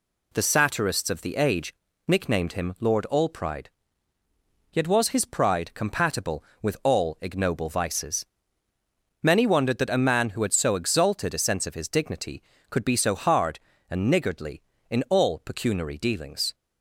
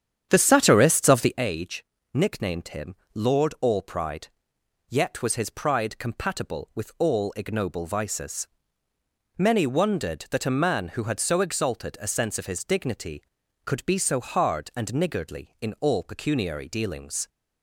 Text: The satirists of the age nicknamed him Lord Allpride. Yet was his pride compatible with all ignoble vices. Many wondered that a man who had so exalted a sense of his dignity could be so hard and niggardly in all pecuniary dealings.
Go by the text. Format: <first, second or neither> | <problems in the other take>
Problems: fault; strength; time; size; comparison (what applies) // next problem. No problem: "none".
first | starts louder than the rest; strong; until 1.4 s; 9 dB // pauses between "age" and "nicknamed"; slight; at 1.8 s; 0.28 s long; slight in the first // pauses between "him" and "Lord"; slight; at 2.9 s; 0.18 s long